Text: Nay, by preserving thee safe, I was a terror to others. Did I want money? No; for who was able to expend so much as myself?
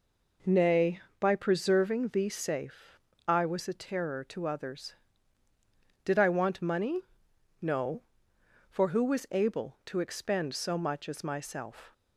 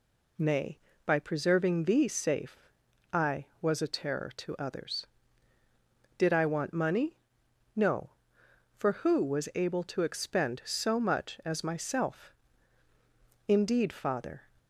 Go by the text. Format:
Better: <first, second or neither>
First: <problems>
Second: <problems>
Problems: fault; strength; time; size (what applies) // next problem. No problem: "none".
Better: first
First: none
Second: goes on to say "Indeed father"; noticeable; from 13.4 s on; 0.96 s long